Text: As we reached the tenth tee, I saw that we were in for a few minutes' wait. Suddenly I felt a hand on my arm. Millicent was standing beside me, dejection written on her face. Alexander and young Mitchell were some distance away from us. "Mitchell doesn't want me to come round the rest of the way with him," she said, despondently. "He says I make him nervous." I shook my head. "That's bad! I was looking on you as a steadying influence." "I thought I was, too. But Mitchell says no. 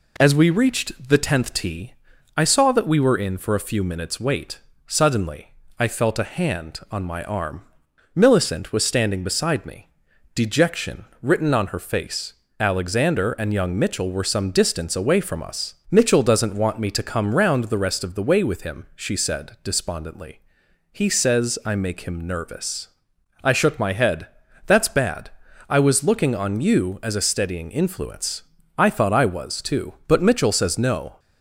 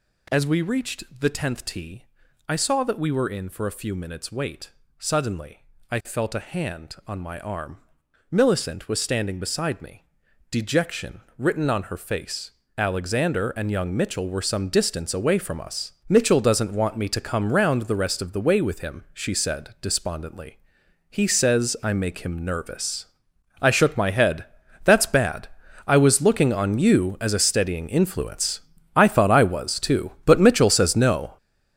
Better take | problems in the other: first | gets louder; strong; throughout; 9.5 dB // pauses between "Suddenly" and "I"; slight; at 5.6 s; 0.28 s long; slight in the first // pauses between "dejection" and "written"; slight; at 11.2 s; 0.16 s long; slight in the first

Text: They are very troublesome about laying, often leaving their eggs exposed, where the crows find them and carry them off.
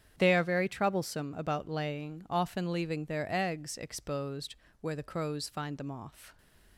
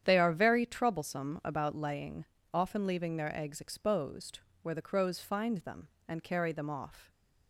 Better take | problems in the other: second | starts louder than the rest; strong; until 1.1 s; 9 dB; strong in the second // skips "and carry them"; at 5.9 s

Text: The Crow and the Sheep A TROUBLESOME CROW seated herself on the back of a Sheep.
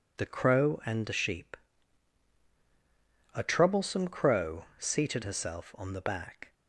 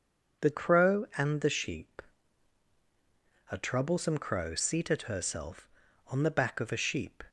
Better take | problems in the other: second | pauses between "Sheep" and "A"; strong; at 1.5 s; 1.7 s long; strong in the second // stops before "of a Sheep"; at 6.5 s

